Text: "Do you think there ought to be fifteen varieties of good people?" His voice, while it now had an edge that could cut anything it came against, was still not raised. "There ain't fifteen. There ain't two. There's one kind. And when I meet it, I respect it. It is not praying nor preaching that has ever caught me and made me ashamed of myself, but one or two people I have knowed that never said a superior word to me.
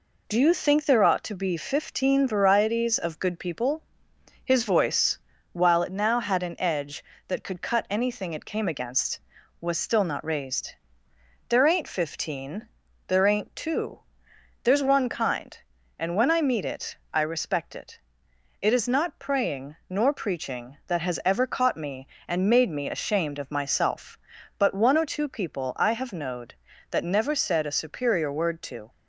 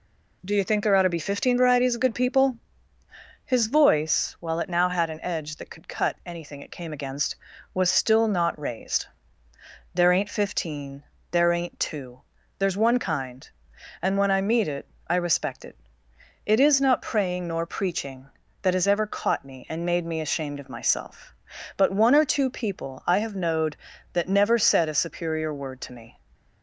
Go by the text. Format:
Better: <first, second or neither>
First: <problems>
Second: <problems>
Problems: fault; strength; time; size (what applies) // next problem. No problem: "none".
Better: second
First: pauses between "praying" and "nor"; slight; at 19.7 s; 0.16 s long // stops before "me"; at 28.8 s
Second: none